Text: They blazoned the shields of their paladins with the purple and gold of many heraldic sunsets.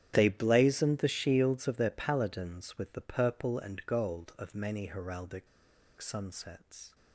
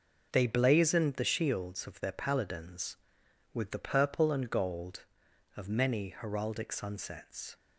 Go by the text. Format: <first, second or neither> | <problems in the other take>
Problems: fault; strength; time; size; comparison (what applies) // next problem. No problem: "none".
second | starts louder than the rest; strong; until 1.1 s; 9.5 dB // pauses between "heraldic" and "sunsets"; noticeable; at 5.4 s; 0.52 s long